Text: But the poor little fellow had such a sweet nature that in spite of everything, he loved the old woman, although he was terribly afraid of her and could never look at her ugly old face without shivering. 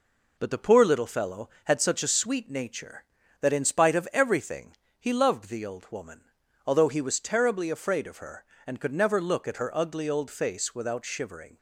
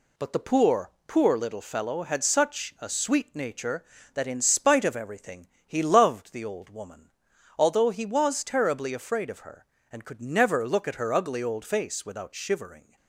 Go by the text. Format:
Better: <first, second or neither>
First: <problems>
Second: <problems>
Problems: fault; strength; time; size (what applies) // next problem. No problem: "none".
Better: first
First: none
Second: says "poor" twice; at 1.0 s